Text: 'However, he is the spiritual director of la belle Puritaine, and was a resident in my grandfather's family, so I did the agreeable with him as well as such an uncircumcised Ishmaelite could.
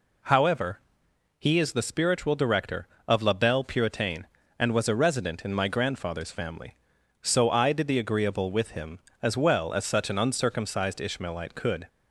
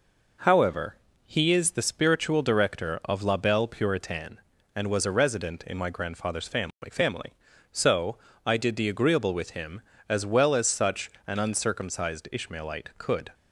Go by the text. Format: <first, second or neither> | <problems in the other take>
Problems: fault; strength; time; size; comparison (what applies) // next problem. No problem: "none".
first | says "family" twice; at 6.8 s // pauses between "so" and "I"; slight; at 8.1 s; 0.28 s long // pauses between "such" and "an"; slight; at 11.1 s; 0.16 s long